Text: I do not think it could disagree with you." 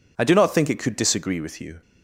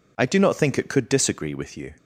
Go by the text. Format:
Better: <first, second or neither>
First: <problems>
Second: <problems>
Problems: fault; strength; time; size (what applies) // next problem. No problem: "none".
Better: neither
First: none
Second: none